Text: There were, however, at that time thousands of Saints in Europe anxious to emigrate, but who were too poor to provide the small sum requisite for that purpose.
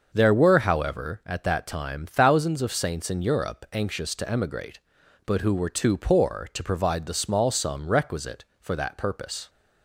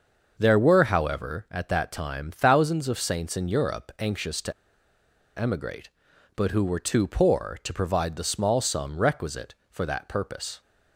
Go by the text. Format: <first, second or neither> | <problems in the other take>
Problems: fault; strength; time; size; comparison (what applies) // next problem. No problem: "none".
first | starts louder than the rest; until 1.3 s; 6.5 dB; also in the first // pauses between "to" and "emigrate"; noticeable; at 4.5 s; 0.85 s long